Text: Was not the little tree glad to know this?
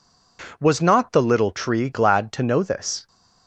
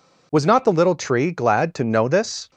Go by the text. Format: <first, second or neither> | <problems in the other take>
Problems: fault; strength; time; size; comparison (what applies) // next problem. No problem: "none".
neither | none